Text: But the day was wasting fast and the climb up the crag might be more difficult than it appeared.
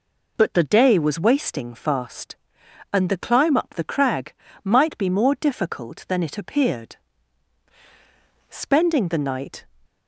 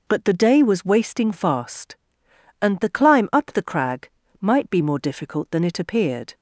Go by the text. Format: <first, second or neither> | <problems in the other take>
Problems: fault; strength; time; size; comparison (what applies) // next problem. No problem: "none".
second | pauses between "crag" and "might"; slight; at 4.3 s; 0.30 s long; slight in the second // goes on to say "Spending the night"; noticeable; from 8.4 s on; 1.1 s long